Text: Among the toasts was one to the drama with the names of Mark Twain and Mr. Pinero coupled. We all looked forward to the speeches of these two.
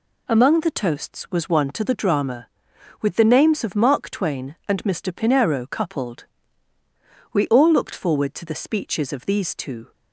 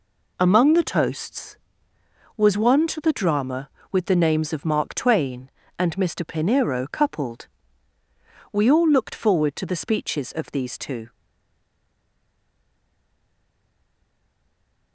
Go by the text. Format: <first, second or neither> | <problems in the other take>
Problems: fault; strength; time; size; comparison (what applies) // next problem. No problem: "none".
first | stays silent after the last word; strong; from 11.1 s on; 3.8 s long